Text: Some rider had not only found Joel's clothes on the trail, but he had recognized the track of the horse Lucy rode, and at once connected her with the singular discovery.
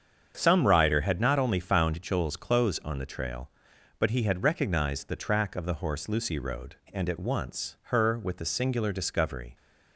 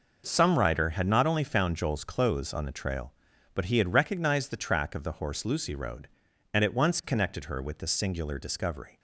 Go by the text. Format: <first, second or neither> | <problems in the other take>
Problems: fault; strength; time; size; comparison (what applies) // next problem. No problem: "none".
second | starts louder than the rest; strong; until 1.4 s; 7.5 dB // skips "connected"; at 7.8 s